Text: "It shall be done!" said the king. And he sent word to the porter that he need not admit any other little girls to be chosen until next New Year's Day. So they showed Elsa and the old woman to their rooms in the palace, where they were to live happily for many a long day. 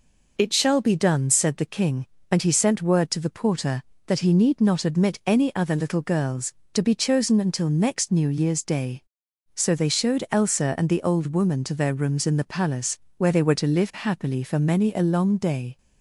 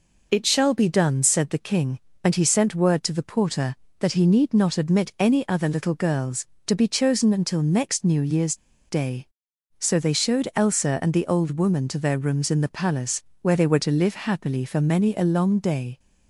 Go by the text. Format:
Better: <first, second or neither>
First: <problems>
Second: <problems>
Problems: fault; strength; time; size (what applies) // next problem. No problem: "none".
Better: first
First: none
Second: pauses between "Year's" and "Day"; slight; at 8.5 s; 0.33 s long